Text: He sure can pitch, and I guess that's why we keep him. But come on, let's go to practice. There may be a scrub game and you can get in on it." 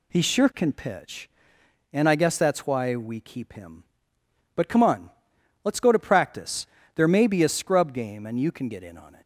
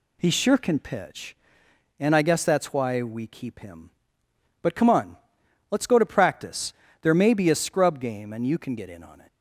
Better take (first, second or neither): neither